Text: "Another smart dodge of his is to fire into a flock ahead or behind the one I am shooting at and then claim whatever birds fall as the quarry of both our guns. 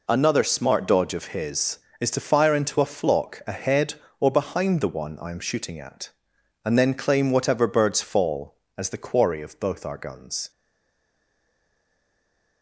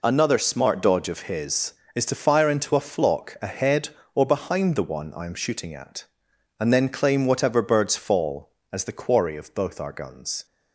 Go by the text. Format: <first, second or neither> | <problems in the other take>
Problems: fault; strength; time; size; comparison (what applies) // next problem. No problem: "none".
second | stays silent after the last word; from 10.5 s on; 2.1 s long